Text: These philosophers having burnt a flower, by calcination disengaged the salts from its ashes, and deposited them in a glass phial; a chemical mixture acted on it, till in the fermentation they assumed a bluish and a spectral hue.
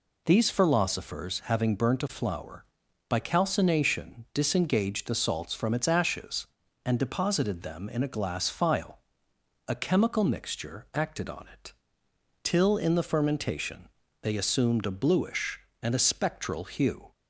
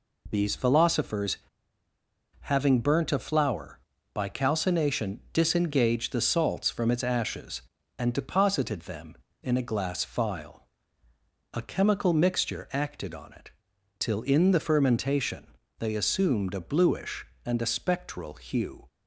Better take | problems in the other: first | pauses between "philosophers" and "having"; at 1.3 s; 1.0 s long // pauses between "fermentation" and "they"; slight; at 15.4 s; 0.32 s long; slight in the first

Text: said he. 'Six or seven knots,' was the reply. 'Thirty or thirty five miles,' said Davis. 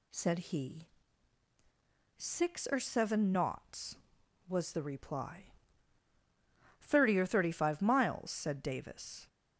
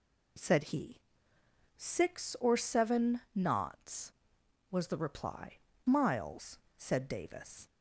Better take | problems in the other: first | skips "Thirty or thirty five"; at 5.7 s

